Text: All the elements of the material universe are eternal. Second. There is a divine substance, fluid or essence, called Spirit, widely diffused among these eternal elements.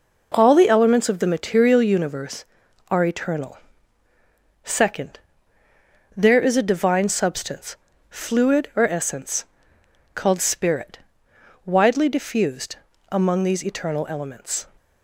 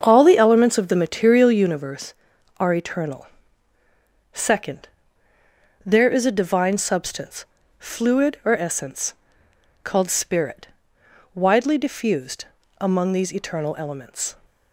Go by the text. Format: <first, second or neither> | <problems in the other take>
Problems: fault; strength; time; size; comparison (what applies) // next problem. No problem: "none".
first | starts louder than the rest; until 1.8 s; 7 dB // pauses between "diffused" and "among"; slight; at 12.4 s; 0.34 s long; slight in the first